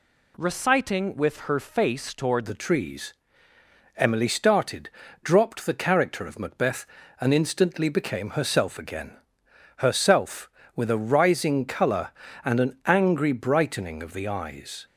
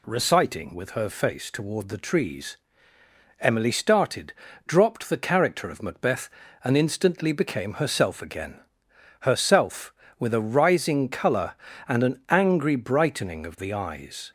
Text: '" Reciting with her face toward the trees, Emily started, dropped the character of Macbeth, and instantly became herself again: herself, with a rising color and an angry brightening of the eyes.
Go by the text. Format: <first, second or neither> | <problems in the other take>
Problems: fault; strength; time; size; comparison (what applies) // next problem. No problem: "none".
second | changes voice from "Reciting" to "toward"; from 0.3 to 2.4 s; 2.1 s long